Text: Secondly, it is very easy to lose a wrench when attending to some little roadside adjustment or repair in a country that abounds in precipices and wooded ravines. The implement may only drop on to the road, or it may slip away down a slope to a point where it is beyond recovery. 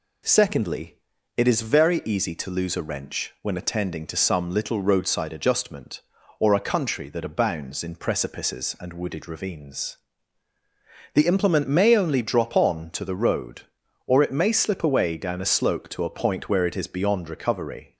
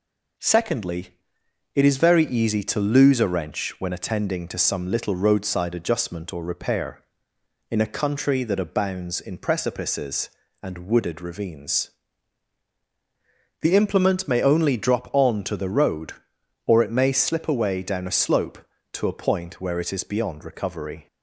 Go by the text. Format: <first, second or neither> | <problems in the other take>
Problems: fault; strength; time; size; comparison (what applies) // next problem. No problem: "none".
second | skips "repair in"; at 6.5 s